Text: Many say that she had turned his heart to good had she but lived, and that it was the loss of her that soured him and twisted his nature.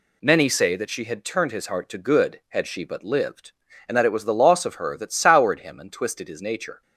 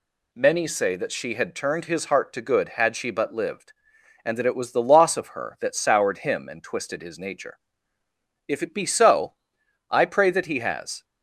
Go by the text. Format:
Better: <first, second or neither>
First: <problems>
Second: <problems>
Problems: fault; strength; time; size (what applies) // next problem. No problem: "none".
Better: first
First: none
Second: goes on to say "If it be so I pray that he has"; strong; from 8.4 s on; 2.5 s long